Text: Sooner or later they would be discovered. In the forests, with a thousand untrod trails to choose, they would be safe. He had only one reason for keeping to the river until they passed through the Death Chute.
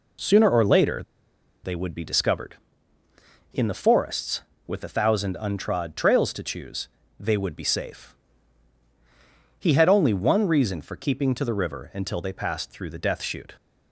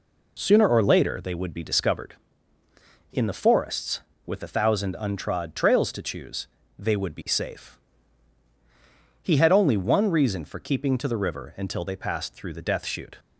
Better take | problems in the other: second | pauses between "later" and "they"; noticeable; at 1.0 s; 0.62 s long

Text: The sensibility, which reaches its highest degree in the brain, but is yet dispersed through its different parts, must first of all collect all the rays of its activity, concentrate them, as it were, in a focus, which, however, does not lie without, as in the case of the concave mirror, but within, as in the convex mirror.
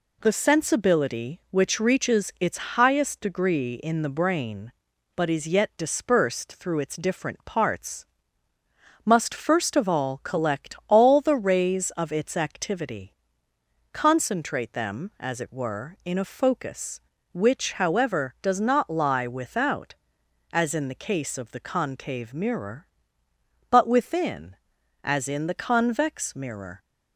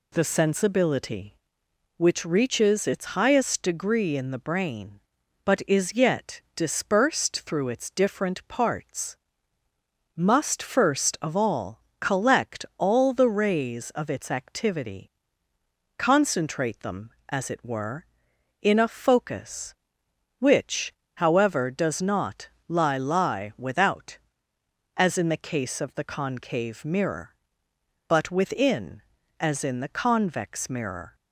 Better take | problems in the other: first | pauses between "all" and "collect"; slight; at 11.8 s; 0.18 s long // pauses between "not" and "lie"; slight; at 22.4 s; 0.22 s long // says "lie" twice; at 22.9 s

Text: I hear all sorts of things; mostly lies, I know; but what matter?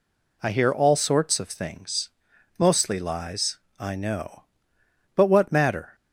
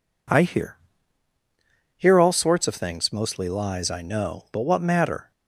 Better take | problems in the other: first | says "hear" twice; at 1.9 s

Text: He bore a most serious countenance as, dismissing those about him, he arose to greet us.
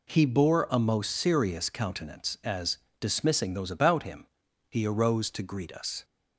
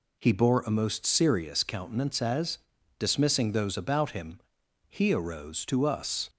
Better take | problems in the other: first | skips "greet"; at 5.8 s

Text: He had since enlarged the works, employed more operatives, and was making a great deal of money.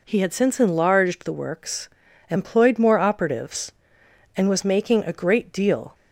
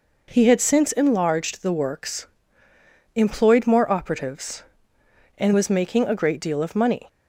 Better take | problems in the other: second | stops before "of money"; at 5.9 s

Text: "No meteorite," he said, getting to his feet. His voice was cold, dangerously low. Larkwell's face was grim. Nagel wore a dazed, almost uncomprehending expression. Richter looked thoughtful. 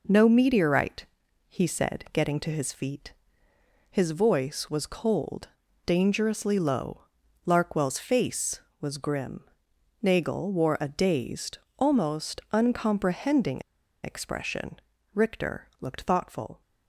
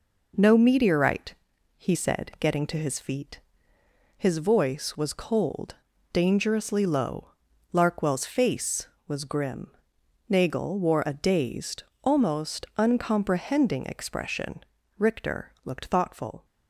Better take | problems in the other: second | pauses between "uncomprehending" and "expression"; at 13.6 s; 0.41 s long

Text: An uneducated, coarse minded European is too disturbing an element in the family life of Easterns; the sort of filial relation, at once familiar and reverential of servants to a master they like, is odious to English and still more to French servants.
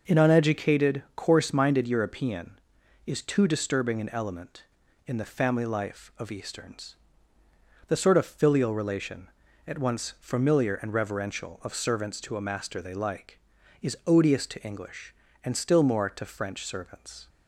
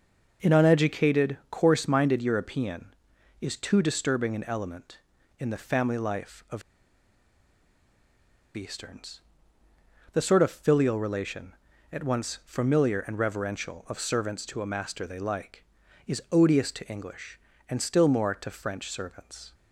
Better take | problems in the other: first | pauses between "of" and "Easterns"; strong; at 6.6 s; 1.9 s long

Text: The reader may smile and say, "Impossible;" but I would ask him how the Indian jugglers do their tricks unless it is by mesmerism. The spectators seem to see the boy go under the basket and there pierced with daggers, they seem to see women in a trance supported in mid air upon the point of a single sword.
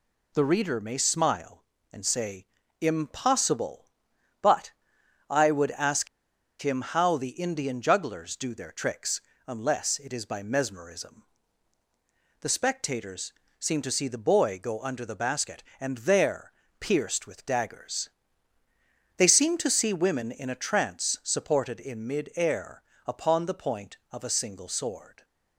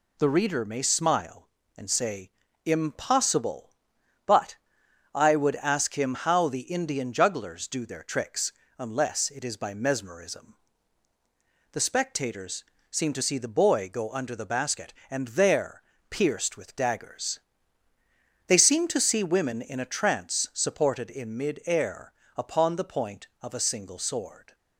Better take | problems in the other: second | pauses between "but" and "I"; noticeable; at 4.7 s; 0.58 s long; noticeable in the second // pauses between "ask" and "him"; noticeable; at 6.0 s; 0.54 s long // pauses between "tricks" and "unless"; slight; at 9.2 s; 0.26 s long; slight in the second // pauses between "spectators" and "seem"; slight; at 13.3 s; 0.26 s long; slight in the second // pauses between "there" and "pierced"; slight; at 16.5 s; 0.28 s long; slight in the second // pauses between "air" and "upon"; slight; at 22.8 s; 0.24 s long; slight in the second

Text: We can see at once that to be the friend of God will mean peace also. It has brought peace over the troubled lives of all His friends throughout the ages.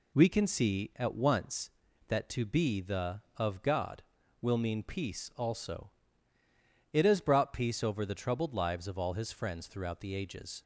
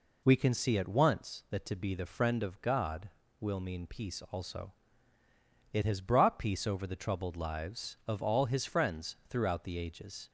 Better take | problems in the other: second | skips "friend"; at 3.2 s

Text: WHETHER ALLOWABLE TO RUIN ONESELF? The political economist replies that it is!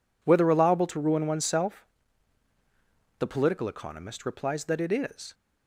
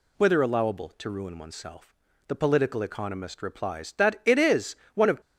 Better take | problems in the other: first | goes on to say "One of"; slight; from 4.9 s on; 0.26 s long

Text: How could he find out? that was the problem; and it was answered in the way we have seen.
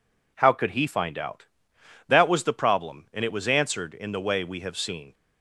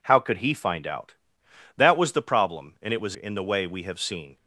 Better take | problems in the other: first | skips "answered"; at 3.1 s

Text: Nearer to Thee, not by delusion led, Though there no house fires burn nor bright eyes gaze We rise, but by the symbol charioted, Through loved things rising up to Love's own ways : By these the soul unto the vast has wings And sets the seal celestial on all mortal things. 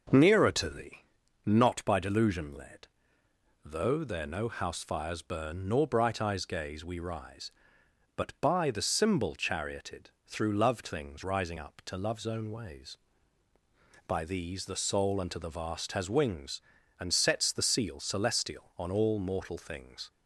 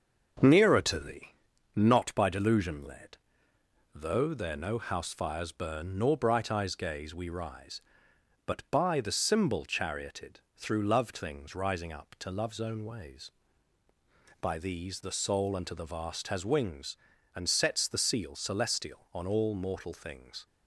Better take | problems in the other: first | gets quieter; throughout; 3.5 dB

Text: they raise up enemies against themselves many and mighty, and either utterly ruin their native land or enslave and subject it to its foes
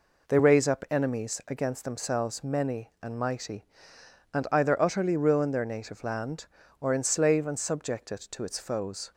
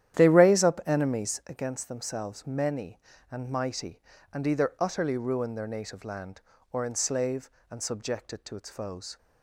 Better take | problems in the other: first | starts louder than the rest; strong; until 1.5 s; 11 dB

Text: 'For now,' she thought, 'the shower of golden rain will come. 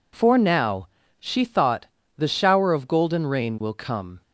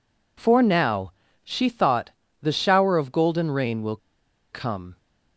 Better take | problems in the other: first | pauses between "will" and "come"; noticeable; at 3.9 s; 0.55 s long

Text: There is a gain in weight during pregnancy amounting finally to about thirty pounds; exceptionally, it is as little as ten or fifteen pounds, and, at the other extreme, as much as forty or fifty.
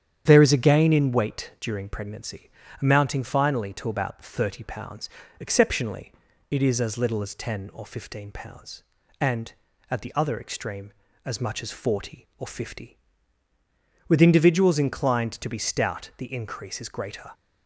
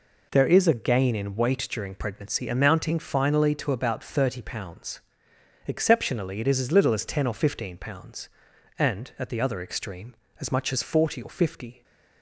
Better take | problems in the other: second | starts louder than the rest; strong; until 1.2 s; 9 dB // pauses between "pregnancy" and "amounting"; slight; at 2.5 s; 0.32 s long // goes on to say "With individuals inclined to be stout the increase is greater"; strong; from 14.0 s on; 3.2 s long

